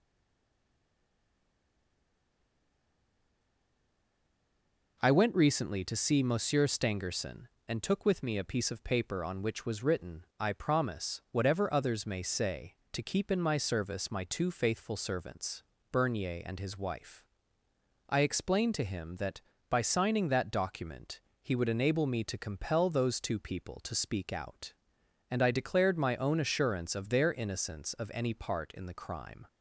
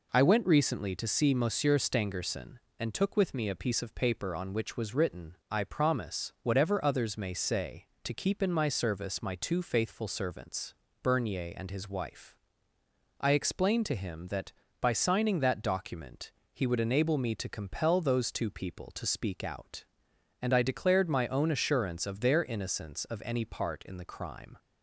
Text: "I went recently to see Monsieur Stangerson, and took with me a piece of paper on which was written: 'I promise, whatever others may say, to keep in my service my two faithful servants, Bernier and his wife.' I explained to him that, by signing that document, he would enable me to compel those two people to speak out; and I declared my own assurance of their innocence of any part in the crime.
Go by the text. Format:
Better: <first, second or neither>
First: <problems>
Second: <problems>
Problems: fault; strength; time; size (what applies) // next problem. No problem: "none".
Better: second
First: stays silent before the first word; strong; until 4.9 s; 4.9 s long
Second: none